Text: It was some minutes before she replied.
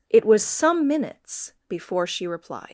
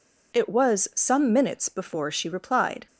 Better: second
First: leaves "replied" unfinished; at 2.6 s; 110 ms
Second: none

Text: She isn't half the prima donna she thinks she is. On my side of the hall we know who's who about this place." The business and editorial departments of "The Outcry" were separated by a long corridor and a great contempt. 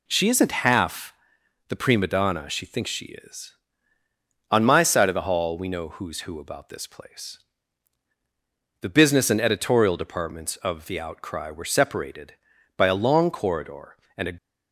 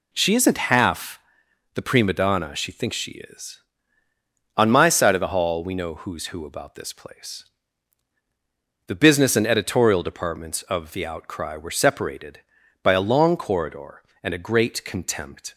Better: second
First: pauses between "half" and "the"; noticeable; at 1.1 s; 0.56 s long // stops before "great contempt"; at 14.3 s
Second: pauses between "half" and "the"; noticeable; at 1.1 s; 0.56 s long

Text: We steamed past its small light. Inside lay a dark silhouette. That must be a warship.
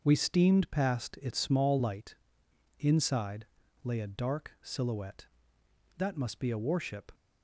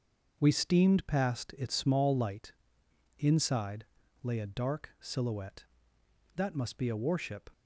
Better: neither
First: starts louder than the rest; until 1.0 s; 6 dB // pauses between "Inside" and "lay"; slight; at 3.4 s; 0.36 s long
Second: starts louder than the rest; until 1.3 s; 6 dB // pauses between "Inside" and "lay"; slight; at 3.8 s; 0.36 s long

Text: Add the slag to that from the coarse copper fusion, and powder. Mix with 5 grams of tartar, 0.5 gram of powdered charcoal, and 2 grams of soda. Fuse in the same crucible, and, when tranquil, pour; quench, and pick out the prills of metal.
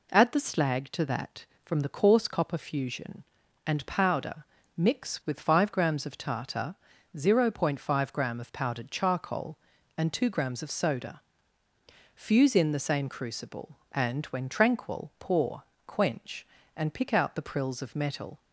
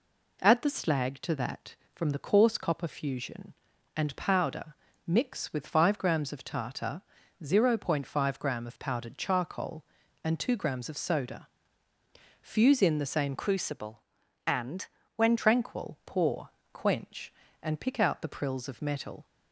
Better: first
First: none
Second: changes voice from "crucible" to "when"; from 13.3 to 15.3 s; 2.0 s long

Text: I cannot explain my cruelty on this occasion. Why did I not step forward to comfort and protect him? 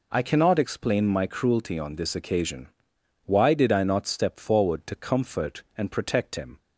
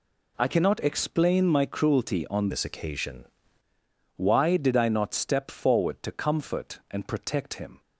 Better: first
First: none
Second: changes voice from "this" to "occasion"; from 2.5 to 3.2 s; 0.7 s long

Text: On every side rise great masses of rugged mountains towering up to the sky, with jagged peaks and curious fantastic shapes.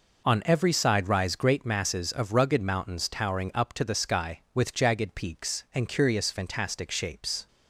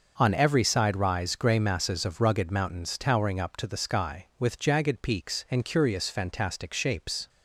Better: first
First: none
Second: starts louder than the rest; noticeable; until 1.1 s; 6 dB // says "grey" for "great"; at 1.3 s

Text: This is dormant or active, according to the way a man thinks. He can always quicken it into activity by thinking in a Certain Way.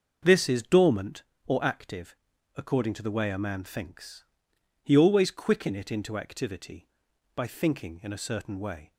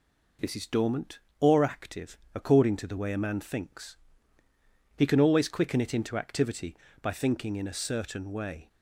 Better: second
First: starts louder than the rest; until 1.5 s; 6 dB // skips "can"; at 4.9 s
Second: none

